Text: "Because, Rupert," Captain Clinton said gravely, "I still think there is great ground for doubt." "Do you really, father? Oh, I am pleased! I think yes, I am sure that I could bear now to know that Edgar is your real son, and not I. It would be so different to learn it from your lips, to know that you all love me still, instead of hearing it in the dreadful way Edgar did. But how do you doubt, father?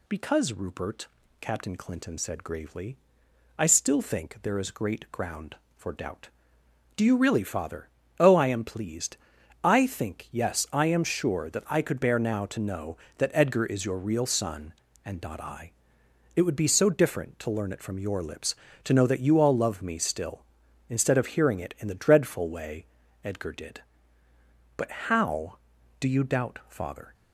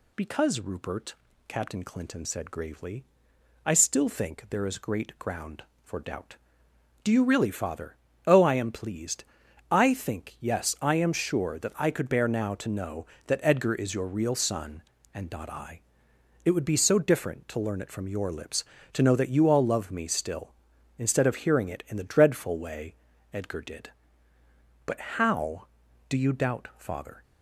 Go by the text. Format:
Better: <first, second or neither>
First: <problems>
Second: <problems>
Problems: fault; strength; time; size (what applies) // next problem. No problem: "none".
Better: neither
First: pauses between "way" and "Edgar"; slight; at 22.8 s; 0.36 s long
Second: pauses between "way" and "Edgar"; slight; at 22.9 s; 0.36 s long